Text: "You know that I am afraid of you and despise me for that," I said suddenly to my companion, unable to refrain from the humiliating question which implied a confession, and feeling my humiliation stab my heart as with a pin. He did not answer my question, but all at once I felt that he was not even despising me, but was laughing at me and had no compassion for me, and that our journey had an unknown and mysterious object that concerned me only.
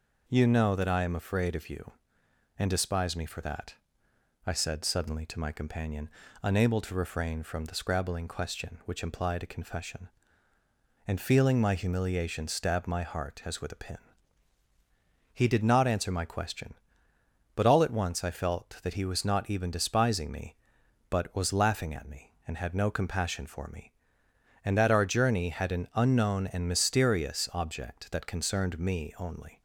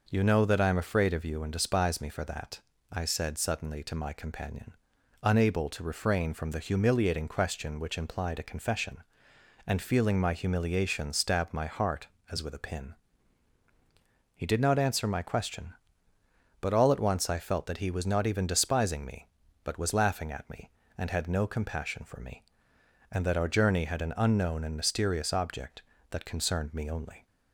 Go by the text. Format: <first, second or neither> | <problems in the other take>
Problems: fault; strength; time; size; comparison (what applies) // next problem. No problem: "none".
second | says "scrabbling" for "humiliating"; at 7.7 s